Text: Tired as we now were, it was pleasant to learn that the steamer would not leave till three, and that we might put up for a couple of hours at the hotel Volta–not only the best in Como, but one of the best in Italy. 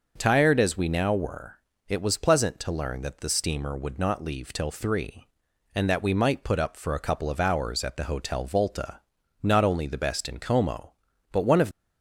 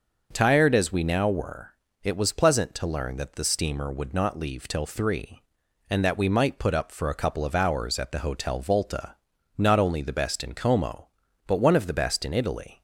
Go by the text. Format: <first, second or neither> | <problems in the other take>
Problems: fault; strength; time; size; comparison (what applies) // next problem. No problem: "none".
second | starts louder than the rest; noticeable; until 1.1 s; 6 dB; noticeable in the second // stops before "the best in Italy"; at 11.7 s